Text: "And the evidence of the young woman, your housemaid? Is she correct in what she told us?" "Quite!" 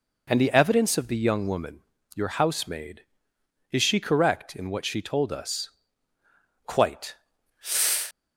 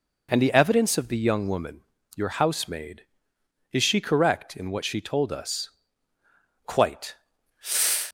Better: neither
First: none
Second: none

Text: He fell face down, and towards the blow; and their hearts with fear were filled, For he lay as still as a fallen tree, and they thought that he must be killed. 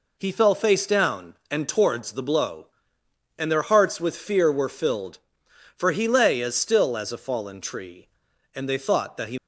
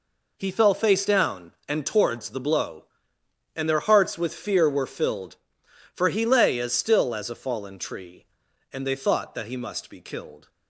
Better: second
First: stops before "must be killed"; at 9.3 s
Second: none

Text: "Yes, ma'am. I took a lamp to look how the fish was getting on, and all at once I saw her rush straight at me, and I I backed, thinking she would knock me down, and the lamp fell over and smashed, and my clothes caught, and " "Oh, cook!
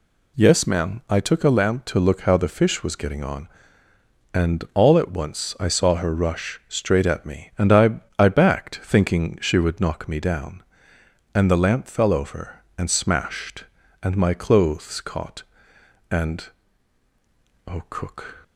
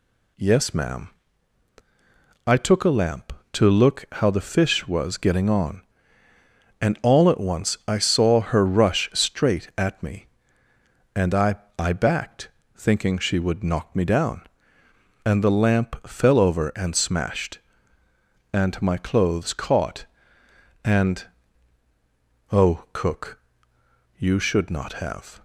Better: first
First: pauses between "I" and "I"; slight; at 8.0 s; 0.18 s long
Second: pauses between "I" and "I"; slight; at 11.5 s; 0.22 s long // goes on to say "you should not have"; noticeable; from 24.1 s on; 1.2 s long

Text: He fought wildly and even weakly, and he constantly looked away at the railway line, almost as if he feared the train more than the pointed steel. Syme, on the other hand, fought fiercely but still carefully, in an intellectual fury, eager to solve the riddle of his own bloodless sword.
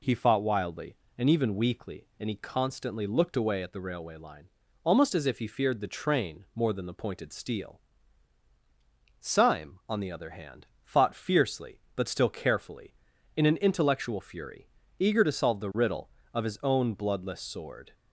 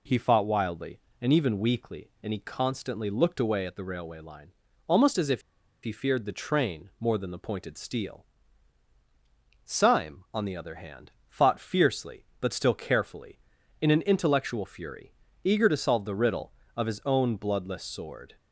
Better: first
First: none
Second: pauses between "if" and "he"; at 5.4 s; 0.42 s long

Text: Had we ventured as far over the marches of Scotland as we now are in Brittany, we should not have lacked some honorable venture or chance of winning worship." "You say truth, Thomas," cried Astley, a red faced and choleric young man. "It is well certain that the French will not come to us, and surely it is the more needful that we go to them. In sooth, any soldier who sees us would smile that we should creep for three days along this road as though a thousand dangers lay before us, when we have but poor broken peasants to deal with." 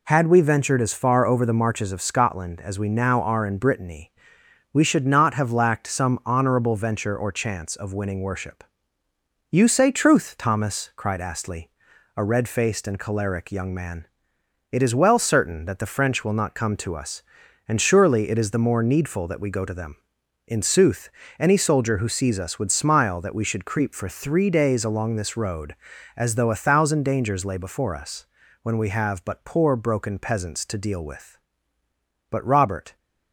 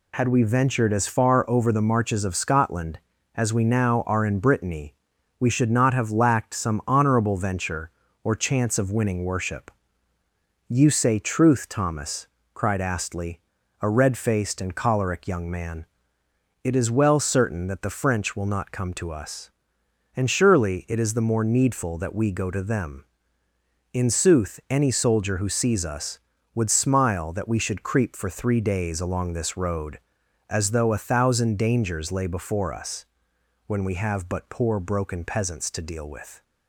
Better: second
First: goes on to say "But Robert"; noticeable; from 32.3 s on; 0.64 s long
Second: none

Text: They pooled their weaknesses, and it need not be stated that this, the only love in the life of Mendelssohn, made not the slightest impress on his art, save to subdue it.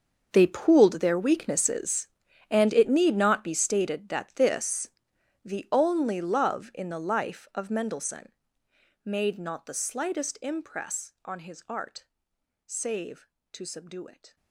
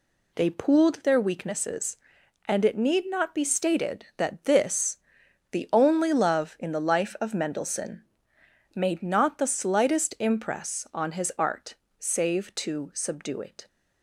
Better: second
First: gets quieter; strong; throughout; 17.5 dB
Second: none

